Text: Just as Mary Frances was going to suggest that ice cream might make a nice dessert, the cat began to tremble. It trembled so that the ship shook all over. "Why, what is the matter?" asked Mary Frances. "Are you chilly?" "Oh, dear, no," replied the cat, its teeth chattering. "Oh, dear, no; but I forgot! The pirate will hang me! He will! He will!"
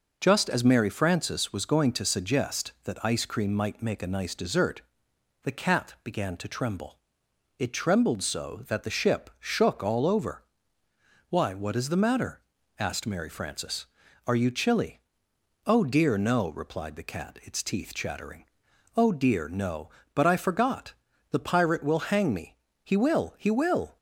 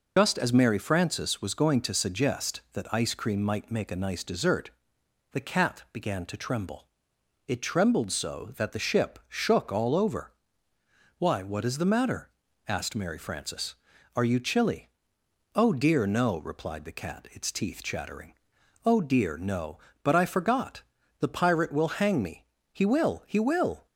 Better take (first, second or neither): first